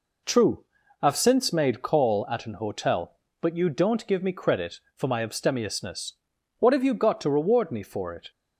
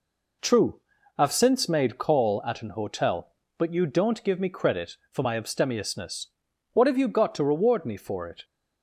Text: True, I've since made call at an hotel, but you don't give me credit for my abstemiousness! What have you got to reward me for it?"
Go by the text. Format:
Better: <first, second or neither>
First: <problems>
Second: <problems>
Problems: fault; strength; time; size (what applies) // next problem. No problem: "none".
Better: neither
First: none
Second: none